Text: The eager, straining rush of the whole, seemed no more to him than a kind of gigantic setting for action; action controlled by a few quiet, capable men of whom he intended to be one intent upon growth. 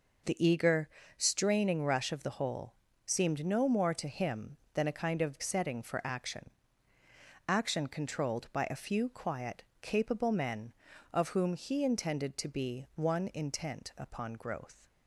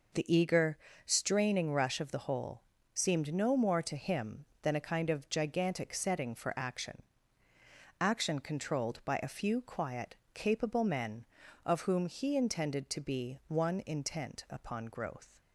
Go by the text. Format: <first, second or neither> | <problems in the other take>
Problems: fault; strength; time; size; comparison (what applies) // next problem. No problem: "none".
second | skips "gigantic"; at 5.4 s